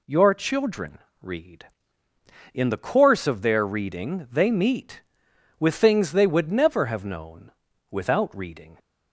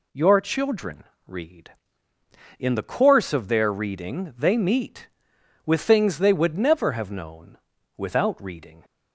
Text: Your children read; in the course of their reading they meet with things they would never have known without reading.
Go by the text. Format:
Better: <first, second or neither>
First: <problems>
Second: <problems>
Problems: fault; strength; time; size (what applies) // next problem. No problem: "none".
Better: neither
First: pauses between "children" and "read"; slight; at 0.9 s; 0.24 s long // pauses between "known" and "without"; at 7.5 s; 0.38 s long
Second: pauses between "children" and "read"; slight; at 1.0 s; 0.24 s long // pauses between "known" and "without"; at 7.5 s; 0.38 s long